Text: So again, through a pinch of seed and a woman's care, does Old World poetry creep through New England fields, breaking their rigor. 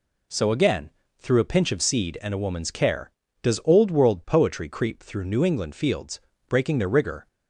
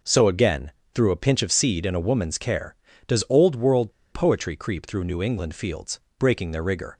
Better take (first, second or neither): first